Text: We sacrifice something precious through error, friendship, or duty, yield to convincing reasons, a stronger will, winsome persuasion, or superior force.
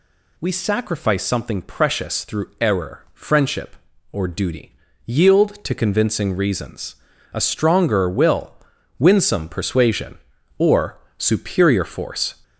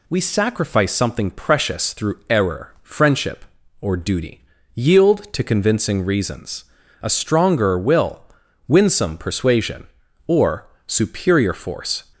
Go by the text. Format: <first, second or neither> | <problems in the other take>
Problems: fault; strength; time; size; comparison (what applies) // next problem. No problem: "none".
second | gets louder; slight; throughout; 3 dB // pauses between "or" and "superior"; slight; at 10.9 s; 0.18 s long; slight in the second